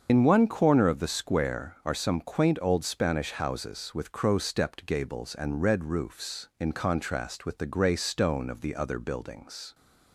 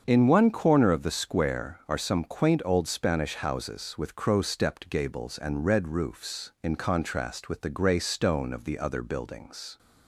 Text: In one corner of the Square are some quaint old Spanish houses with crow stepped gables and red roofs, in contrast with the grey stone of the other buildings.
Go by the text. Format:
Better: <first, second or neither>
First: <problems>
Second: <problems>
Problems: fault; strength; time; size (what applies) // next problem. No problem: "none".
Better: second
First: loses the start of "In"; at 0.0 s; 70 ms // starts louder than the rest; until 1.1 s; 7 dB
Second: starts louder than the rest; until 1.0 s; 7 dB